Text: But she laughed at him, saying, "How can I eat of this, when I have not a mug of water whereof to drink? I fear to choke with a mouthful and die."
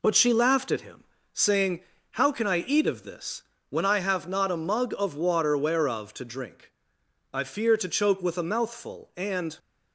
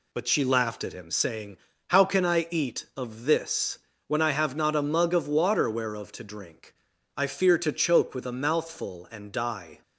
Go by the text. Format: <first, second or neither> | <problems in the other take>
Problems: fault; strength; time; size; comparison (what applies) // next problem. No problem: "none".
second | stops before "die"; at 9.5 s